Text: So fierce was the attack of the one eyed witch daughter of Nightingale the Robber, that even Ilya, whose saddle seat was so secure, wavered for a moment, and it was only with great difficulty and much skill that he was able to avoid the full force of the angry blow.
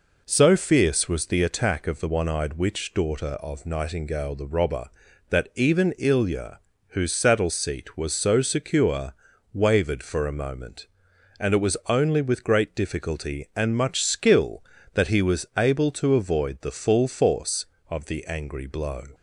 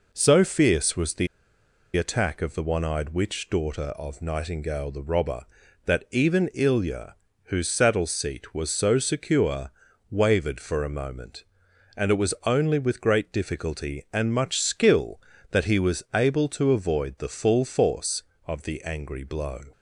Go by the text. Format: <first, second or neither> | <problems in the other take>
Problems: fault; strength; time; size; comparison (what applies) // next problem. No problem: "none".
first | pauses between "the" and "attack"; noticeable; at 1.2 s; 0.69 s long